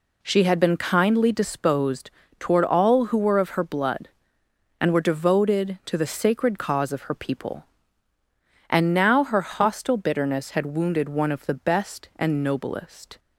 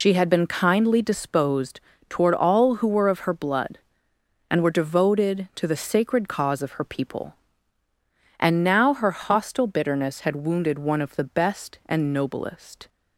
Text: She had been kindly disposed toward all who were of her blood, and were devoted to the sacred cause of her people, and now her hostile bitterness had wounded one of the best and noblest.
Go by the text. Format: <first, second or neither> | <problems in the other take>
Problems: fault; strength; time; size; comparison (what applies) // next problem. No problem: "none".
first | loses the start of "She"; at 0.0 s; 80 ms // pauses between "disposed" and "toward"; slight; at 1.8 s; 0.28 s long; slight in the first